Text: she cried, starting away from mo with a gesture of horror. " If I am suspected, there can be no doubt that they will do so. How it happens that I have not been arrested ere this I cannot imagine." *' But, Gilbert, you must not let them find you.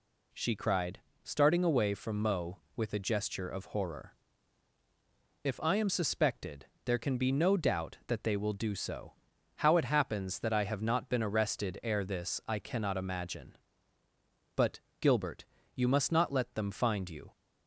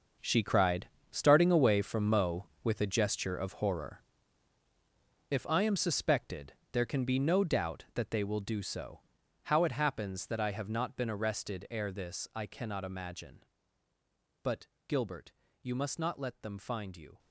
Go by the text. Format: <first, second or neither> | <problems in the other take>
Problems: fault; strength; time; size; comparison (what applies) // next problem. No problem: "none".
first | gets quieter; strong; throughout; 13.5 dB